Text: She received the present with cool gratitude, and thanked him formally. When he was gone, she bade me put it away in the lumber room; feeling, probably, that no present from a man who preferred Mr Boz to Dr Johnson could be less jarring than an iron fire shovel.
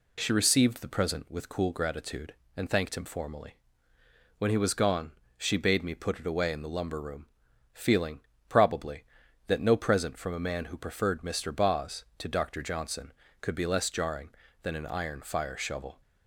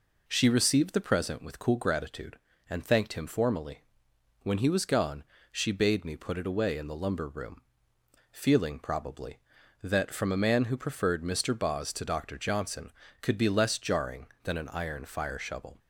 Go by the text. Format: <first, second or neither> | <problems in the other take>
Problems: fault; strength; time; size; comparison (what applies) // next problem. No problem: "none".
first | skips "no present"; at 10.1 s